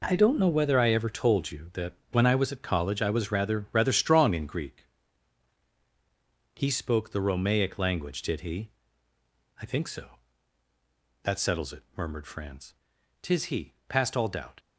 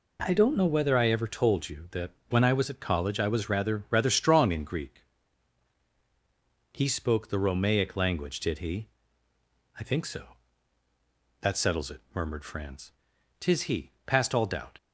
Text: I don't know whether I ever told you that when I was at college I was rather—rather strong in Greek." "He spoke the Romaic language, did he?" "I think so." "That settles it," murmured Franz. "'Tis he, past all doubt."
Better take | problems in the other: second | gets quieter; strong; throughout; 10.5 dB // pauses between "that" and "when"; slight; at 1.9 s; 0.18 s long; slight in the second

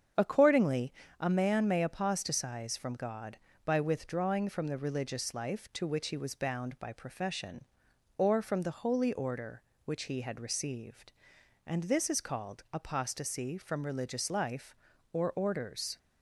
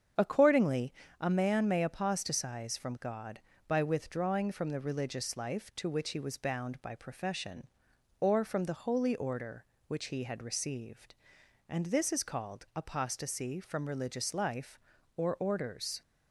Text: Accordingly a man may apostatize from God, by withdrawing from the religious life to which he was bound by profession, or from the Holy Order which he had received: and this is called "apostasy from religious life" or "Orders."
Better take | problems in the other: neither | starts louder than the rest; strong; the same in both // pauses between "Accordingly" and "a"; slight; the same in both

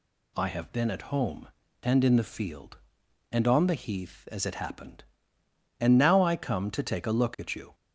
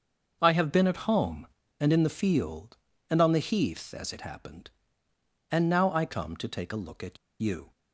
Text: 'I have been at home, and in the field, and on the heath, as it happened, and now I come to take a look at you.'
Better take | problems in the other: first | starts louder than the rest; until 1.4 s; 6.5 dB // pauses between "at" and "you"; slight; at 7.1 s; 0.24 s long

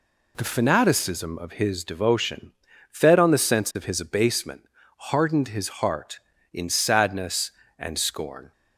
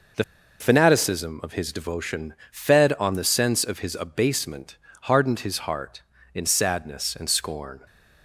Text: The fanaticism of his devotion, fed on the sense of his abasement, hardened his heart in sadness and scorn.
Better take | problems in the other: first | pauses between "The" and "fanaticism"; slight; at 0.2 s; 0.36 s long

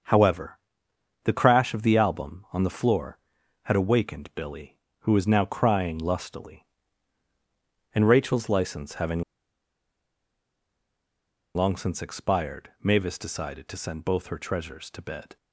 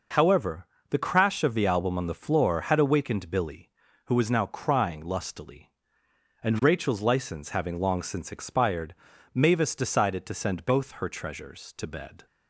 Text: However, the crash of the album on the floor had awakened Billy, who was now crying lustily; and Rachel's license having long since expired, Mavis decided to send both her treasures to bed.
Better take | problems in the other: second | starts louder than the rest; until 1.7 s; 6.5 dB // pauses between "having" and "long"; strong; at 9.2 s; 2.3 s long

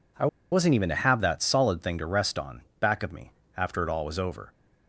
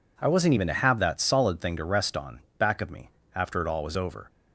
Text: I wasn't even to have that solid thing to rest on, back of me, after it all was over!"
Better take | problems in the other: second | pauses between "I" and "wasn't"; slight; at 0.2 s; 0.25 s long

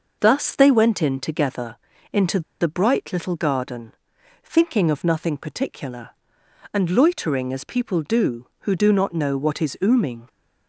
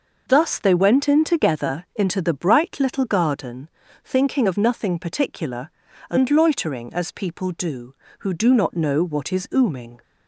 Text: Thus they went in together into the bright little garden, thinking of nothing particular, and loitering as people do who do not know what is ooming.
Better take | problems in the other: second | pauses between "together" and "into"; slight; at 1.7 s; 0.36 s long // pauses between "into" and "the"; slight; at 2.4 s; 0.20 s long

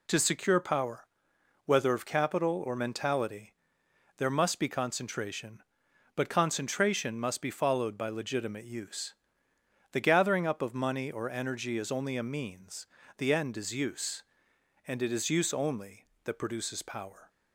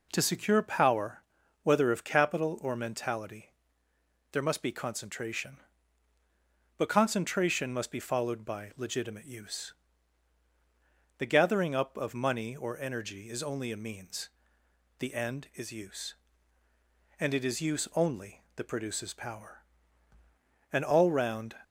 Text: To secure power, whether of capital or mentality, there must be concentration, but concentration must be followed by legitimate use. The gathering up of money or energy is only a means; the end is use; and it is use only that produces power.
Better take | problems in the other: first | goes on to say "An all round"; noticeable; from 20.7 s on; 0.86 s long

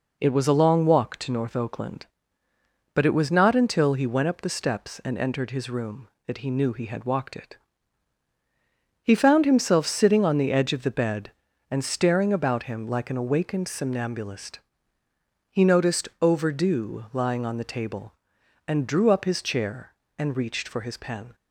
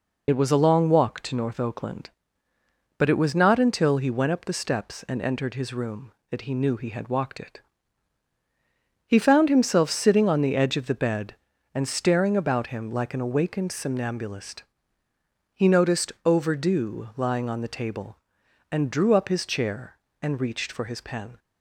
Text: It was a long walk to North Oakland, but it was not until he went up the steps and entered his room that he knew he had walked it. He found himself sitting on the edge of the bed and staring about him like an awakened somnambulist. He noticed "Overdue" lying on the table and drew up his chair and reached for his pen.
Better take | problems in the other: first | loses the start of "It"; at 0.2 s; 35 ms

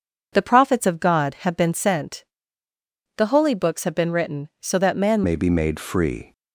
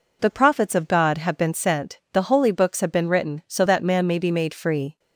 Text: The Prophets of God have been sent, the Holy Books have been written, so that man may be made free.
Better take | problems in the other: second | changes voice at "may"; from 5.2 s on; 1.1 s long

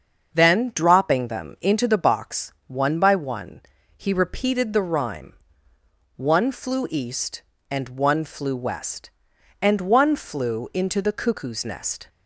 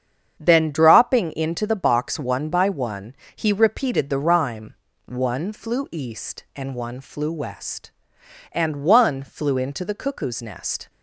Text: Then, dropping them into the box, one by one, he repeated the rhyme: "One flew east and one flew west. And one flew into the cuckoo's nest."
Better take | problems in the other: first | starts louder than the rest; strong; until 1.4 s; 7.5 dB; also in the first // skips "them"; at 1.3 s

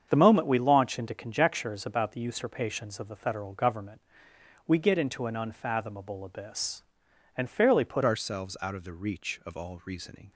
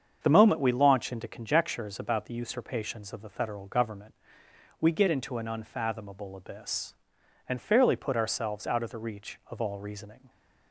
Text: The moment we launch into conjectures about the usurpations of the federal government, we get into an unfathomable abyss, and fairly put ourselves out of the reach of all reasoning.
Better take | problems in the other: second | starts louder than the rest; strong; until 1.1 s; 7.5 dB; strong in the second // changes voice at "ourselves"; from 8.0 s on; 2.3 s long

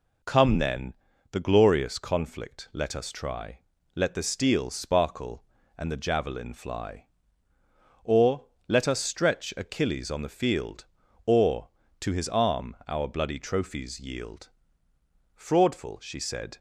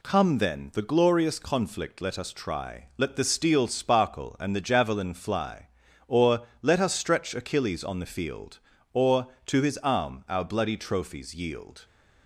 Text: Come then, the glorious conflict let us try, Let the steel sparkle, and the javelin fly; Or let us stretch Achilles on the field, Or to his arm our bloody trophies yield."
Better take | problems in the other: second | pauses between "Or" and "let"; slight; at 8.4 s; 0.22 s long; slight in the second // goes on to say "Fraudful she said"; noticeable; from 15.3 s on; 1.2 s long

